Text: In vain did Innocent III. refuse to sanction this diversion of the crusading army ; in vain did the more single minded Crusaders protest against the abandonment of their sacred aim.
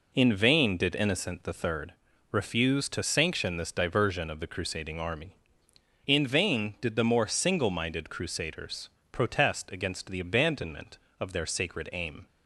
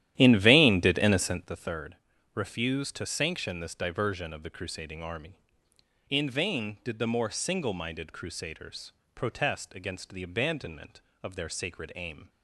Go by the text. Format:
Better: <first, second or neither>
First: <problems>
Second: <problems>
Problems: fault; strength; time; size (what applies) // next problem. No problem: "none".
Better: first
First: pauses between "Crusaders" and "protest"; slight; at 8.9 s; 0.20 s long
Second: starts louder than the rest; strong; until 1.6 s; 12 dB // pauses between "Crusaders" and "protest"; slight; at 8.9 s; 0.20 s long